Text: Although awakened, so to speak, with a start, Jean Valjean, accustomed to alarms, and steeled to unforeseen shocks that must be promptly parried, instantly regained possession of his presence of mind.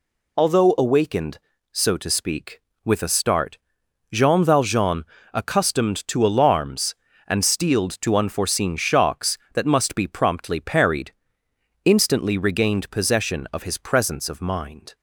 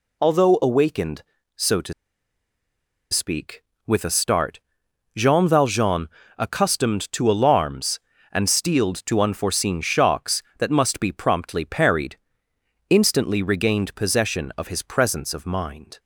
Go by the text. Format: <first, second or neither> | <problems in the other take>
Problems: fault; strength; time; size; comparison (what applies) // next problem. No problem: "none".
first | pauses between "to" and "speak"; at 1.9 s; 1.1 s long